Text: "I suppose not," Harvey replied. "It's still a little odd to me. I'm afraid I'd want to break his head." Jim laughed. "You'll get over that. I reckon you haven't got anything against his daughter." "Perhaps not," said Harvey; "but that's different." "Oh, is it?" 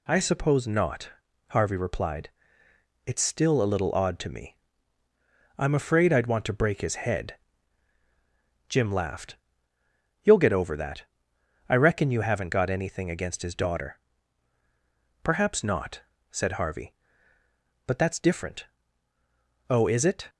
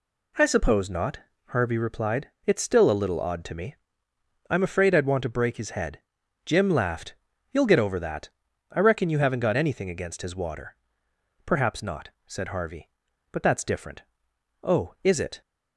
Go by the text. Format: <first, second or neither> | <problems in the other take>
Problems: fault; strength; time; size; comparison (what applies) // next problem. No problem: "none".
first | says "water" for "daughter"; at 10.3 s